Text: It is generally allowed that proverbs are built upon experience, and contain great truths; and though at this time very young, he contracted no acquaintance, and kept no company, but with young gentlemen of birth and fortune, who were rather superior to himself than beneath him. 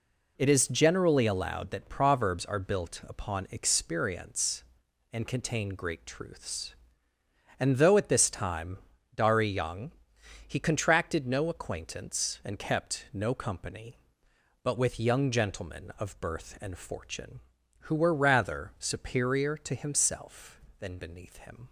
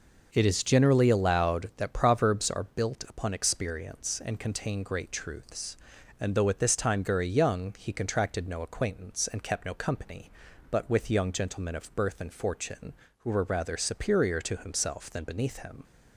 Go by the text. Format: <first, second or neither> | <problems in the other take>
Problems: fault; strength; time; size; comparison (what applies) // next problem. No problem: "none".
second | says "dari" for "very"; at 9.1 s